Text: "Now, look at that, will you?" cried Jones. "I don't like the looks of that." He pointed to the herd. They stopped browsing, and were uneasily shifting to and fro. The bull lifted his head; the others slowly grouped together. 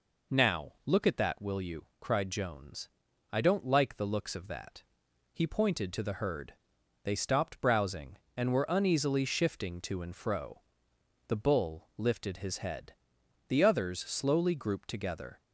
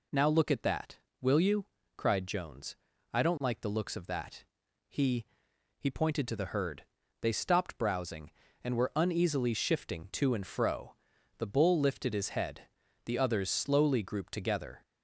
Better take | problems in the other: first | says "He" twice; at 5.7 s

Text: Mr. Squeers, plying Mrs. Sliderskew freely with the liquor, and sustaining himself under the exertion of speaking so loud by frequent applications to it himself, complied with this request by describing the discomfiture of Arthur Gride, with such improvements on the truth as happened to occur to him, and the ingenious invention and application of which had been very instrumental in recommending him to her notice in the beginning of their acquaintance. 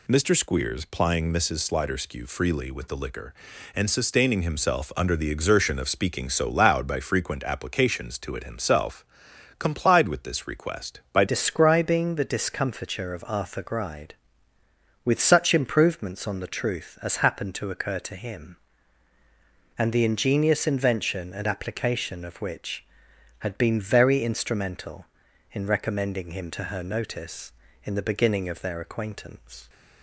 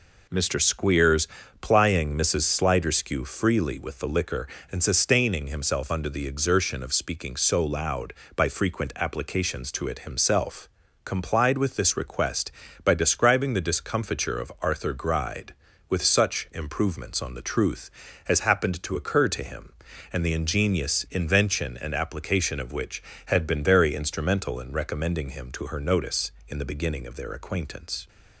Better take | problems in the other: second | changes voice at "describing"; from 11.2 s on; 18.4 s long

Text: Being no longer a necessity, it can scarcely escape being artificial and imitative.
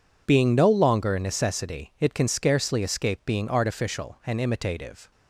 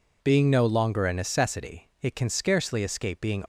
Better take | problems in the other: first | stops before "artificial and imitative"; at 3.4 s

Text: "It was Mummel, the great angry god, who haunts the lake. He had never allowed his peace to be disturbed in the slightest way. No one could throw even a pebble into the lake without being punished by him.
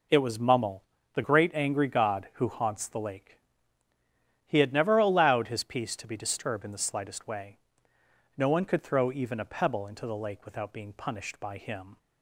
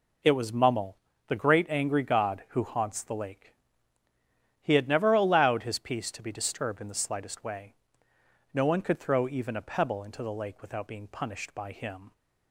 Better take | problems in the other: neither | none

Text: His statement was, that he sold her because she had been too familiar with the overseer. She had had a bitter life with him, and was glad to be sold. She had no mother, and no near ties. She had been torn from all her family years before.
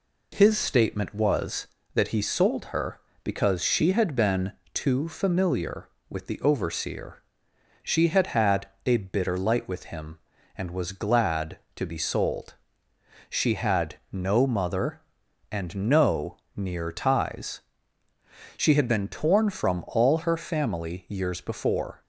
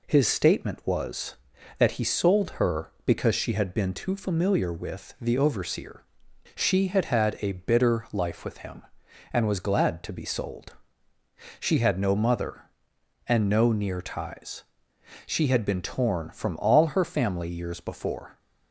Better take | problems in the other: second | pauses between "been" and "too"; slight; at 4.5 s; 0.20 s long // pauses between "had" and "a"; slight; at 8.6 s; 0.20 s long // says "light" for "life"; at 9.3 s // pauses between "no" and "near"; slight; at 16.3 s; 0.18 s long

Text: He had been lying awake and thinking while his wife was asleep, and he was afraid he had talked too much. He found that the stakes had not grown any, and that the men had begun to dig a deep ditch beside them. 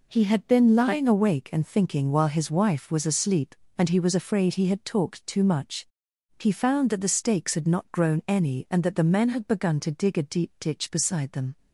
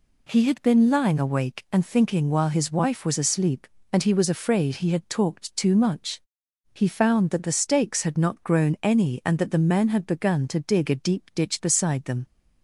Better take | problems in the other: neither | none

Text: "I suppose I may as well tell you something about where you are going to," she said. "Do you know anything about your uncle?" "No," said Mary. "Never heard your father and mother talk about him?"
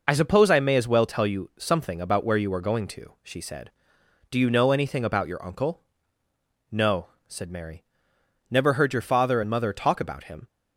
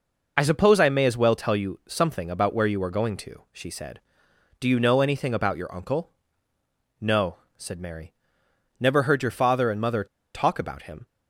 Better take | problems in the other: first | pauses between "mother" and "talk"; slight; at 10.0 s; 0.29 s long

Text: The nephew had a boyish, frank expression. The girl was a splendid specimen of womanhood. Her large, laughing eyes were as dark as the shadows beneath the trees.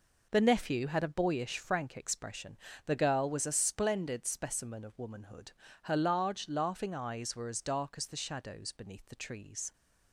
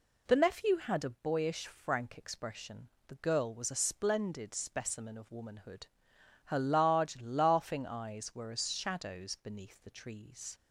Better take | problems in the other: first | skips "dark as the"; at 8.7 s

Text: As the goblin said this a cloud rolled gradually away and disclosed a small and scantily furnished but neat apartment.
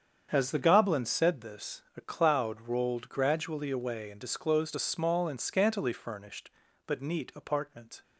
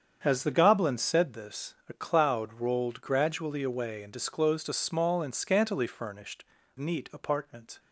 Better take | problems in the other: first | starts louder than the rest; strong; until 1.2 s; 7.5 dB; strong in the first // skips "but"; at 6.6 s

